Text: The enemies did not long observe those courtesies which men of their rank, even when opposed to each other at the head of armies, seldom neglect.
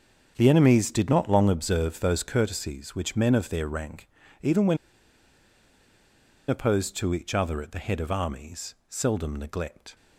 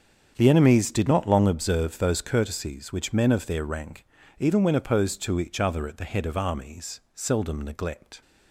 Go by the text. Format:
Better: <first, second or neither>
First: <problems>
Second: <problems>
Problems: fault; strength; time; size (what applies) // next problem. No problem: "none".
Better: second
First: starts louder than the rest; strong; until 1.3 s; 7 dB // pauses between "when" and "opposed"; strong; at 4.7 s; 1.7 s long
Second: starts louder than the rest; strong; until 1.3 s; 7.5 dB